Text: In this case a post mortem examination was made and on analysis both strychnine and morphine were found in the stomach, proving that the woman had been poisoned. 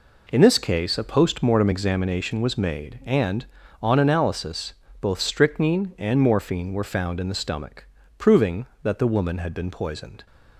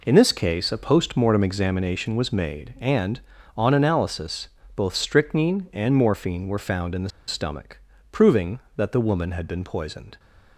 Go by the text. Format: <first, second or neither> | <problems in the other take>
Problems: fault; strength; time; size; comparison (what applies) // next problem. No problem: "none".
first | pauses between "analysis" and "both"; slight; at 4.4 s; 0.26 s long; slight in the first // pauses between "the" and "stomach"; slight; at 7.0 s; 0.18 s long